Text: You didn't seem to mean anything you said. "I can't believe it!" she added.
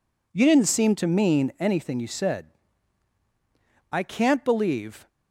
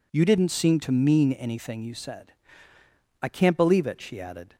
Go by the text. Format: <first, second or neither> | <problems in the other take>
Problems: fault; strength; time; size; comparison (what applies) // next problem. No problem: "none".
second | stops before "it she added"; at 5.0 s